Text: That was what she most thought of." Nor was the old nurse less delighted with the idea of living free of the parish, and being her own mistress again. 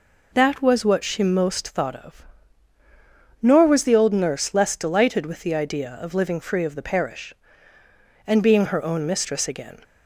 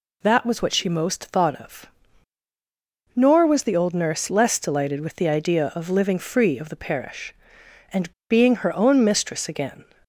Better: first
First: none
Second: pauses between "and" and "being"; slight; at 8.1 s; 0.17 s long

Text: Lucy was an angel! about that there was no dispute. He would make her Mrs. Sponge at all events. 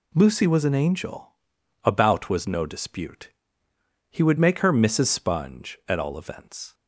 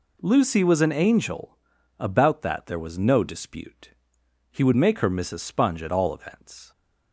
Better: second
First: skips "that there"; at 2.2 s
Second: none

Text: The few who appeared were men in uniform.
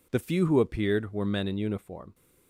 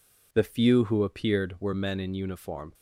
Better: neither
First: none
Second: none

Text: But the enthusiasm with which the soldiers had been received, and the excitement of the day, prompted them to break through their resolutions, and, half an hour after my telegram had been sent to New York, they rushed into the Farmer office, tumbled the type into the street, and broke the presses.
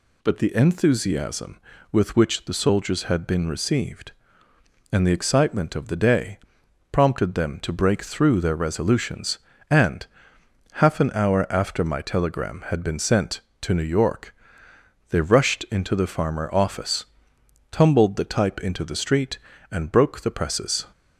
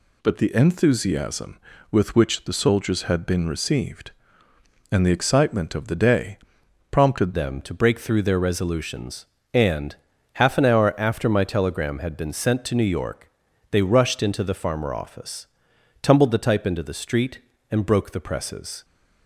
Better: first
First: none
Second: changes voice at "them"; from 7.3 s on; 11.5 s long

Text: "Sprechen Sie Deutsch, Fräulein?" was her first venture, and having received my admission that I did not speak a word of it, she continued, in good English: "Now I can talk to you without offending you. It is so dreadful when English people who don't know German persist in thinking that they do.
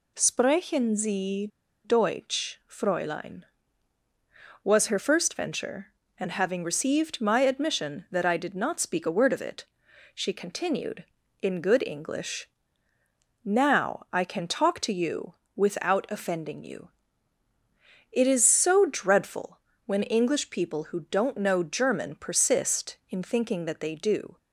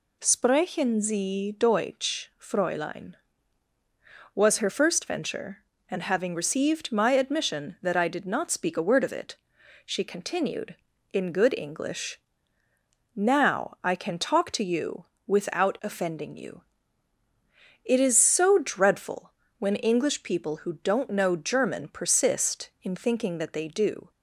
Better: second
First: pauses between "Sie" and "Deutsch"; at 1.4 s; 0.37 s long // pauses between "you" and "without"; slight; at 15.3 s; 0.20 s long // pauses between "dreadful" and "when"; slight; at 19.5 s; 0.26 s long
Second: pauses between "you" and "without"; slight; at 15.0 s; 0.20 s long // pauses between "dreadful" and "when"; slight; at 19.3 s; 0.26 s long

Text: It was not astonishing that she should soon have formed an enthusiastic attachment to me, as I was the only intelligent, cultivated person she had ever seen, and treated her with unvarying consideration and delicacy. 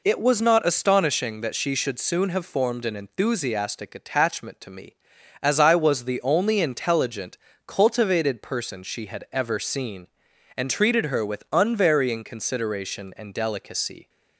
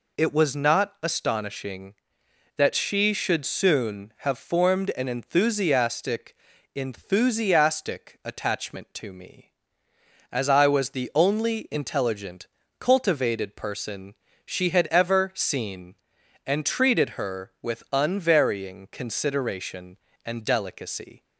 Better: first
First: none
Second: says "enthusiastic" twice; at 6.7 s // pauses between "person" and "she"; slight; at 14.1 s; 0.32 s long

